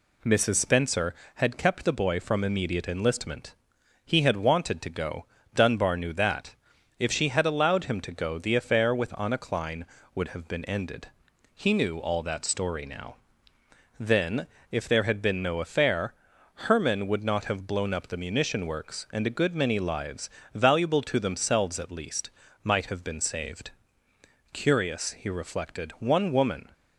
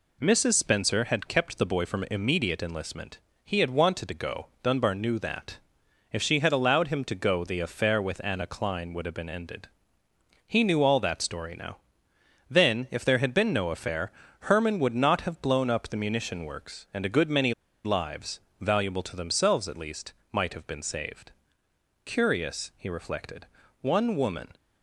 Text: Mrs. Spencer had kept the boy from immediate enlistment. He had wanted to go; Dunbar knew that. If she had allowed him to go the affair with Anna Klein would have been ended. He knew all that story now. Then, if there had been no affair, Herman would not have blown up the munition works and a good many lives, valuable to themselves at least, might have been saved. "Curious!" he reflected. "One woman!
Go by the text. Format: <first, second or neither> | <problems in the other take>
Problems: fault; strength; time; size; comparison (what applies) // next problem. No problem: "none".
first | pauses between "many" and "lives"; slight; at 17.5 s; 0.30 s long